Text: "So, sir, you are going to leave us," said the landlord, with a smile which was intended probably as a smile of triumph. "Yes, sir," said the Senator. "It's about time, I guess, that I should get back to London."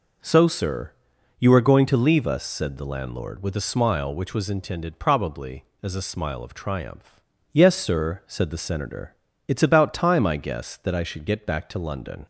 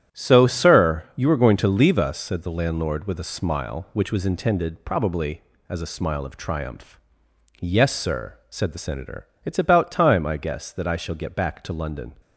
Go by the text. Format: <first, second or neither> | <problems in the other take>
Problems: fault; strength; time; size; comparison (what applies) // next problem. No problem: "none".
first | starts louder than the rest; strong; until 1.2 s; 10.5 dB // says "shall" for "should"; at 10.9 s